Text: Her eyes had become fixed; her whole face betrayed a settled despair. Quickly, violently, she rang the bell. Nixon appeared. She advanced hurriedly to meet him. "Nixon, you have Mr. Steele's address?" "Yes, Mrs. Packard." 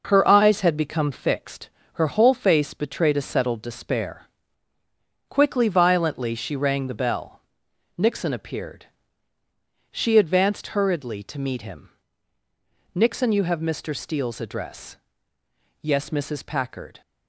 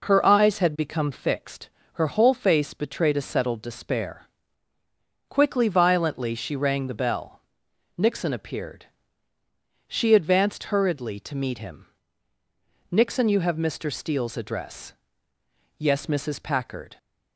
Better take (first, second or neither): second